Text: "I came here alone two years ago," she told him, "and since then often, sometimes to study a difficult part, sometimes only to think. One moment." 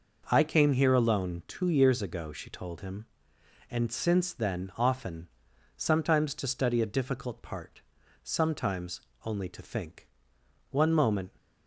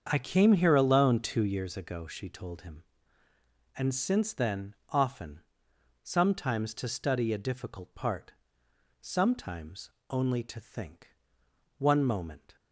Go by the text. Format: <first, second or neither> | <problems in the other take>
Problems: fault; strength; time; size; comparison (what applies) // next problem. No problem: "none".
first | starts louder than the rest; until 1.7 s; 7 dB // pauses between "sometimes" and "only"; slight; at 9.8 s; 0.20 s long; slight in the first